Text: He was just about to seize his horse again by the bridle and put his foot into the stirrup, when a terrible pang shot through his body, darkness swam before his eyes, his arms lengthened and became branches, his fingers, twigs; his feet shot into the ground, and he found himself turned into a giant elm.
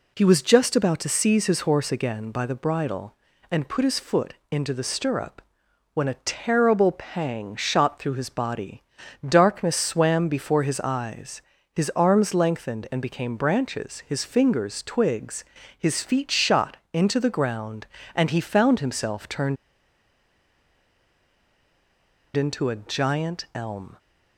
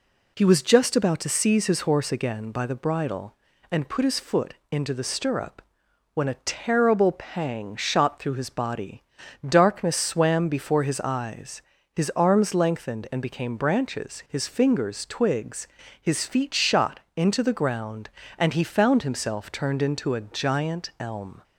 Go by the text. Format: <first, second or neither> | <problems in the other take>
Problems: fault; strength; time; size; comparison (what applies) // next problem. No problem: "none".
second | pauses between "foot" and "into"; slight; at 4.3 s; 0.16 s long; slight in the second // pauses between "shot" and "into"; slight; at 16.7 s; 0.16 s long; slight in the second // pauses between "turned" and "into"; strong; at 19.5 s; 2.7 s long